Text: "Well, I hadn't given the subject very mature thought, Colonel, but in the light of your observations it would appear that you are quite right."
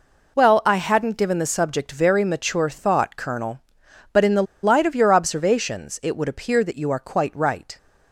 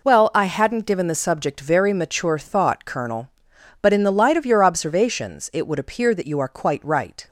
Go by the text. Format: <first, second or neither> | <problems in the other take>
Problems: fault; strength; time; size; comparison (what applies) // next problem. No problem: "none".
second | pauses between "the" and "light"; slight; at 4.4 s; 0.19 s long